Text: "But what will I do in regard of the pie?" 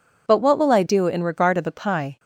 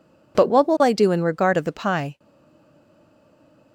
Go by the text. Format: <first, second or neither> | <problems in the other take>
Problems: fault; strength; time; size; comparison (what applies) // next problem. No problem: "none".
first | stays silent after the last word; noticeable; from 2.1 s on; 1.6 s long